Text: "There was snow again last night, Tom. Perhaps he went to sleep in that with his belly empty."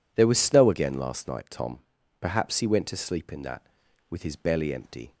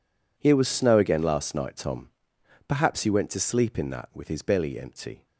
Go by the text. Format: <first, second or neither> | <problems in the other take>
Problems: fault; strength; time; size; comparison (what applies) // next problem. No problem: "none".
first | says "Here" for "There"; at 0.3 s